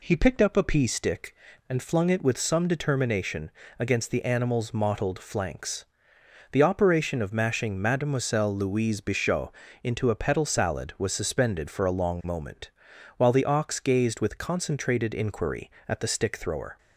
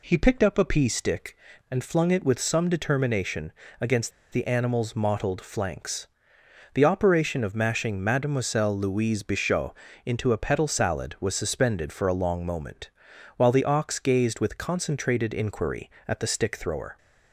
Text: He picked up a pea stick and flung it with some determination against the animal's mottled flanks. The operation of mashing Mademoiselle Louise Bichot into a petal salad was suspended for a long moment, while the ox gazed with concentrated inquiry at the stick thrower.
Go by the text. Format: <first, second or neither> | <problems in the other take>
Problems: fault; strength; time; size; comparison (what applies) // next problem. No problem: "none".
first | pauses between "determination" and "against"; slight; at 3.5 s; 0.28 s long; slight in the first // pauses between "against" and "the"; slight; at 4.1 s; 0.21 s long // pauses between "Bichot" and "into"; slight; at 9.7 s; 0.28 s long; slight in the first